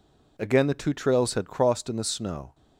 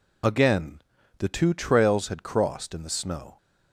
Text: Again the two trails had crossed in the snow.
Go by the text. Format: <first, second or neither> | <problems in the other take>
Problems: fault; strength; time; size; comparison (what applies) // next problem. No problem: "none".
first | loses the start of "Again"; at 0.2 s; 45 ms // pauses between "Again" and "the"; at 0.8 s; 0.38 s long